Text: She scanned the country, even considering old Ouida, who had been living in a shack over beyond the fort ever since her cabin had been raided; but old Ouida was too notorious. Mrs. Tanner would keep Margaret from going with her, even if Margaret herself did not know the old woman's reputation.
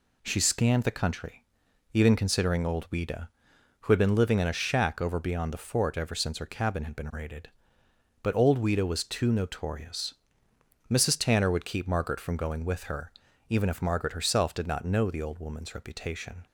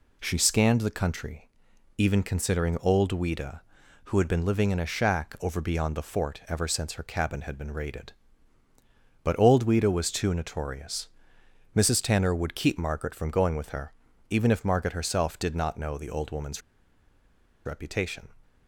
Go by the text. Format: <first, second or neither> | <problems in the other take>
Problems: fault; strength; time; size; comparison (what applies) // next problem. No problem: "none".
first | pauses between "woman's" and "reputation"; at 16.6 s; 1.0 s long